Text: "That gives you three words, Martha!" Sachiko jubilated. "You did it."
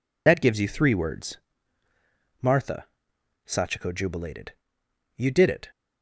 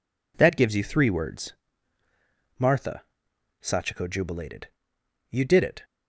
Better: second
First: loses the start of "That"; at 0.2 s; 55 ms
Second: none

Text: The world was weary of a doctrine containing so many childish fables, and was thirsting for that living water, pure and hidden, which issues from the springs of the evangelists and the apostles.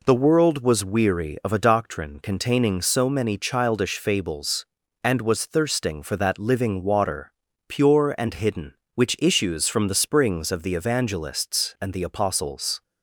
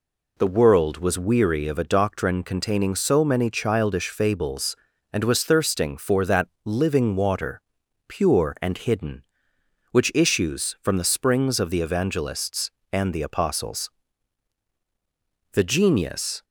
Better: first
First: none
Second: pauses between "that" and "living"; slight; at 6.4 s; 0.16 s long // goes on to say "The genius"; noticeable; from 15.5 s on; 0.90 s long

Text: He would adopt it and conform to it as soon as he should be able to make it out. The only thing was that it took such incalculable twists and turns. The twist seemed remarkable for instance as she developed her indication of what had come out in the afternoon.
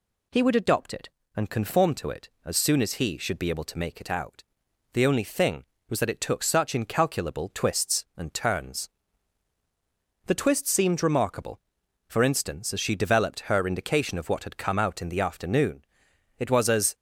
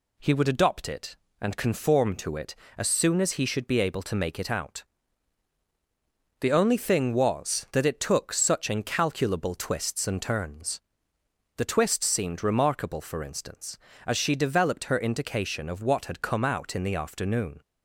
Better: second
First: goes on to say "It was as"; from 16.3 s on; 0.56 s long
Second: none

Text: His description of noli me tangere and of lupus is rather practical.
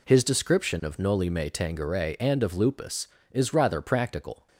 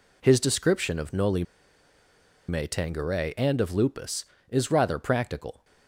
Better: first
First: none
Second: pauses between "noli" and "me"; at 1.4 s; 1.0 s long

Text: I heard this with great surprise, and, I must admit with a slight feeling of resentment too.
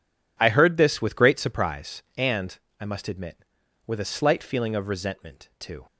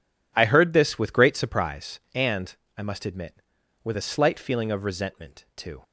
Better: neither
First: none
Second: none

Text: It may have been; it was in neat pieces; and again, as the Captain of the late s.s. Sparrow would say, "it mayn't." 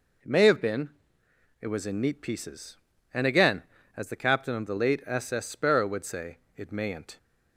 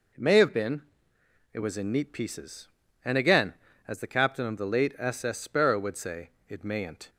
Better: neither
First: none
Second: none

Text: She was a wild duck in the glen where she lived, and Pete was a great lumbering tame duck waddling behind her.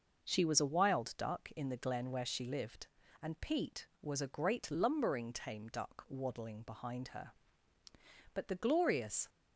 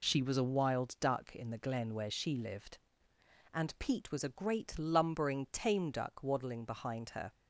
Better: second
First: goes on to say "But the glorious"; noticeable; from 8.3 s on; 0.94 s long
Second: none

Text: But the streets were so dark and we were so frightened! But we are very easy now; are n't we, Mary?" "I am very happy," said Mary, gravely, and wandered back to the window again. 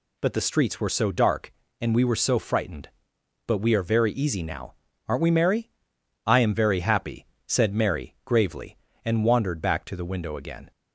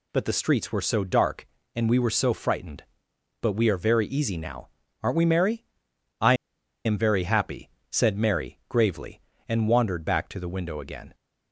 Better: first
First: none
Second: pauses between "I" and "am"; noticeable; at 6.3 s; 0.51 s long

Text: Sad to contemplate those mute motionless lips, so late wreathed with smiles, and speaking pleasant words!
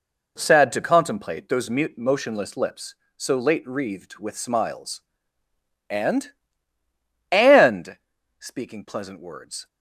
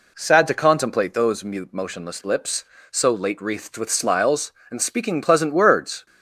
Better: second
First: says "and" twice; at 7.3 s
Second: none

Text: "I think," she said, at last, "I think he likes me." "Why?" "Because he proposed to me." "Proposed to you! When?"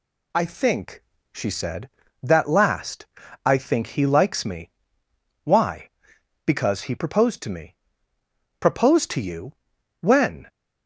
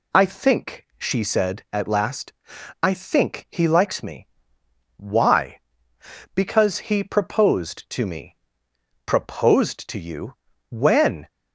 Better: second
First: says "that" for "at"; at 2.2 s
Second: none

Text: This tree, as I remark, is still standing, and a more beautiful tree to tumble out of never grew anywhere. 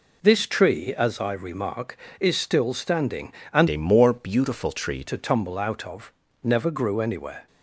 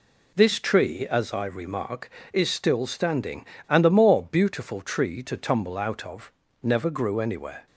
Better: second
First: changes voice from "a" to "tree"; from 3.6 to 5.0 s; 1.4 s long // pauses between "of" and "never"; slight; at 6.1 s; 0.32 s long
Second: pauses between "of" and "never"; slight; at 6.3 s; 0.32 s long

